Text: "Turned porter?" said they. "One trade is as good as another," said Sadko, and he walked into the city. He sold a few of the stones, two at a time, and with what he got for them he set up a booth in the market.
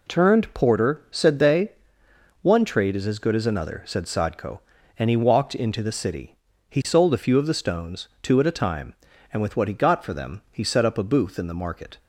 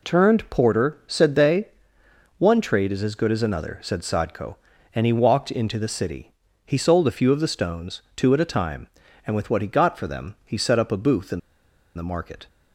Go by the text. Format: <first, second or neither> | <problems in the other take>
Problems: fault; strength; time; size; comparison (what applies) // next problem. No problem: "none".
first | pauses between "in" and "the"; noticeable; at 11.3 s; 0.56 s long